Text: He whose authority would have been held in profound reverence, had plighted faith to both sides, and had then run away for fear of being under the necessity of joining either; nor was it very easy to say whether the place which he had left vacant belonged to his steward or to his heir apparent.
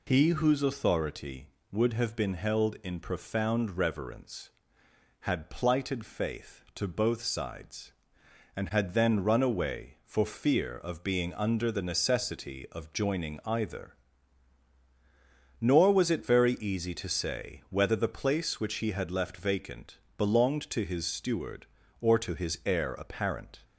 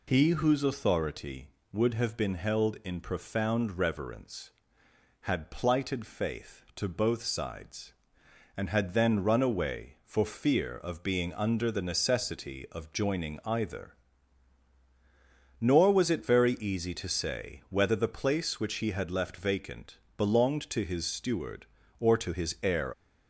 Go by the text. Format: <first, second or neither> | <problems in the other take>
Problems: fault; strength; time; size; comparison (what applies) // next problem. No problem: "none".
first | pauses between "vacant" and "belonged"; slight; at 19.9 s; 0.18 s long; slight in the first // stops before "apparent"; at 22.9 s